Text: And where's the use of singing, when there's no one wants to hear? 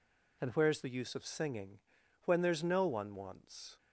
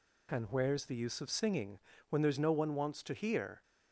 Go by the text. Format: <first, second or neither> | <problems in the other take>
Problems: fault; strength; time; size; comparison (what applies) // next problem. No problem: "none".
second | stops before "to hear"; at 3.7 s